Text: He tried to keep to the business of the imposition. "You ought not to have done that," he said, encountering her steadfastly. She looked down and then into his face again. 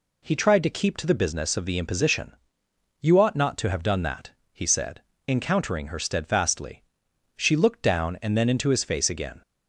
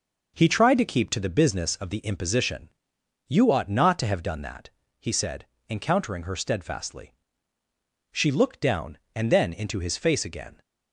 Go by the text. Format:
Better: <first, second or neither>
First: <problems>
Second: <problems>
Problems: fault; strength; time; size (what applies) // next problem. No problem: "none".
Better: neither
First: none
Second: none